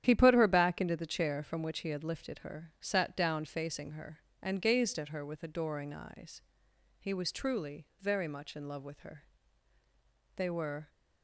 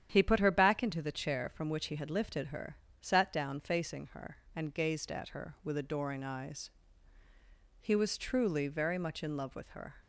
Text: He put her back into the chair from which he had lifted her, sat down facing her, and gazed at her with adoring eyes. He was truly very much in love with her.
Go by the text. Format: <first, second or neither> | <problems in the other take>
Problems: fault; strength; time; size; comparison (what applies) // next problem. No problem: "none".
second | starts louder than the rest; strong; until 1.0 s; 10 dB; strong in the second // pauses between "truly" and "very"; slight; at 7.8 s; 0.16 s long // goes on to say "They were"; from 10.3 s on; 0.54 s long